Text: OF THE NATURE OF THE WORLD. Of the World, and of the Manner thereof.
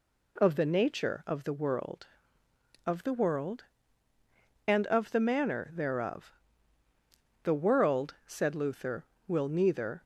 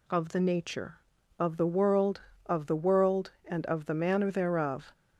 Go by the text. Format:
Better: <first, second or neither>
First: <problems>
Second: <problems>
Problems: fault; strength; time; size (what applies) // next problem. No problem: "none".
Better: second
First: goes on to say "The world said Luther will neither"; strong; from 7.4 s on; 2.5 s long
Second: none